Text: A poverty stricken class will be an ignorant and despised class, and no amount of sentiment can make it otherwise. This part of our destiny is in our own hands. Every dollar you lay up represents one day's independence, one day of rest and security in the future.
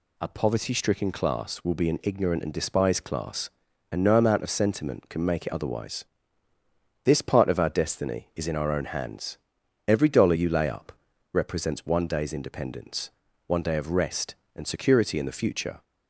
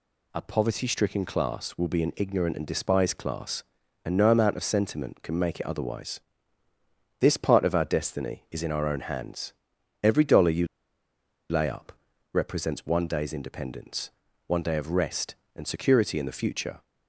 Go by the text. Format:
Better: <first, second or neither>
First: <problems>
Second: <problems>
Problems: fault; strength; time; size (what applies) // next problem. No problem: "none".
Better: first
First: pauses between "up" and "represents"; at 10.9 s; 0.40 s long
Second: pauses between "you" and "lay"; noticeable; at 10.6 s; 0.83 s long // pauses between "up" and "represents"; at 11.9 s; 0.40 s long